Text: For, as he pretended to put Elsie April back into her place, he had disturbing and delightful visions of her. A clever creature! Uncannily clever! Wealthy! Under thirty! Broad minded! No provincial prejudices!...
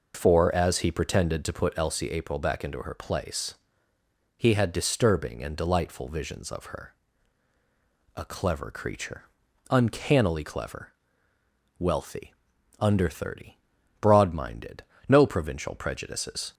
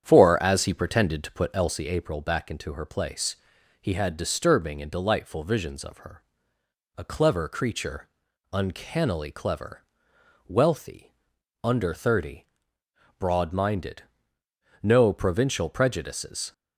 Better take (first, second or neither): first